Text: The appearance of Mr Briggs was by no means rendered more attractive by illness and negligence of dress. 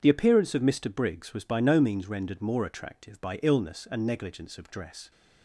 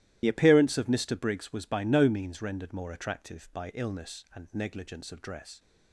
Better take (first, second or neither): first